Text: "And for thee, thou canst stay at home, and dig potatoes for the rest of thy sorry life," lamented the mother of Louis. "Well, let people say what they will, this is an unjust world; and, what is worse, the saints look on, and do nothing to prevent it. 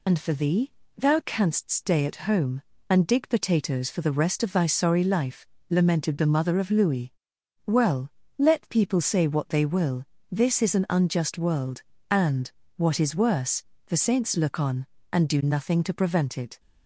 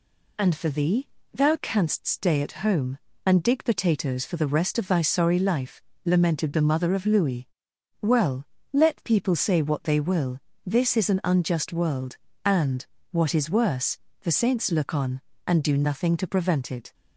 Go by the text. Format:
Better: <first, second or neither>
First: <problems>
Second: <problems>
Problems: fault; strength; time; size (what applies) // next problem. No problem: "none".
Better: second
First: loses the start of "And"; at 0.0 s; 40 ms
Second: none